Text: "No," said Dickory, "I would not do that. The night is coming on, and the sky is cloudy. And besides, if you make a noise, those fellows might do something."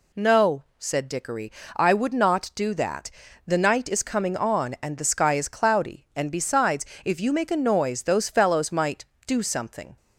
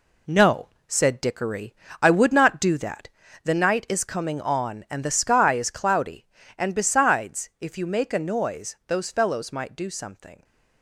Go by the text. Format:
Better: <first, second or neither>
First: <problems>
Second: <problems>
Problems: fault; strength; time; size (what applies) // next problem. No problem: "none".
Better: first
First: none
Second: gets quieter; strong; throughout; 7.5 dB